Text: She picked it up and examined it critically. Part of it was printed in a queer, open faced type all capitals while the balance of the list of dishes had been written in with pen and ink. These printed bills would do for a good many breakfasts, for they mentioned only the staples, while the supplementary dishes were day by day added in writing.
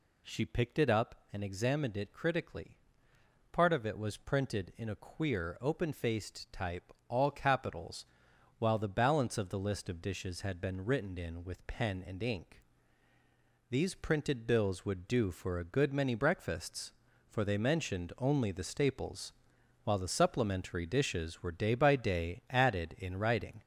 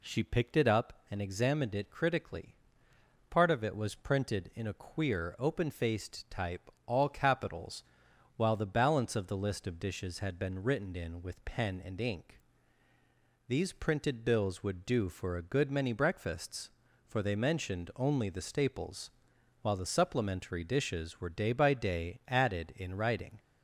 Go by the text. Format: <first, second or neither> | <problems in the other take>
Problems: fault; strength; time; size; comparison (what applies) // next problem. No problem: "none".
second | gets louder; noticeable; throughout; 5 dB // pauses between "type" and "all"; slight; at 6.9 s; 0.18 s long; slight in the second // pauses between "capitals" and "while"; noticeable; at 8.0 s; 0.50 s long; noticeable in the second